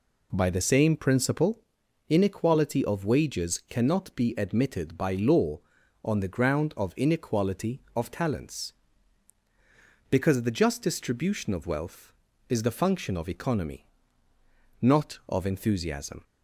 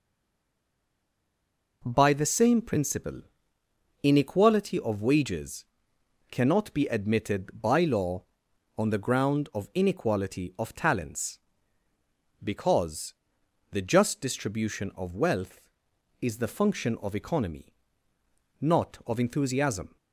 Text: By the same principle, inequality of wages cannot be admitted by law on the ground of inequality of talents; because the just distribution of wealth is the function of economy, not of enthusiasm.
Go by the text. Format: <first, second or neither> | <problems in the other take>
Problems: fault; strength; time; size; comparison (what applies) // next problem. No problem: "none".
first | stays silent before the first word; noticeable; until 1.8 s; 1.8 s long // pauses between "wages" and "cannot"; noticeable; at 5.6 s; 0.66 s long // pauses between "because" and "the"; noticeable; at 13.1 s; 0.58 s long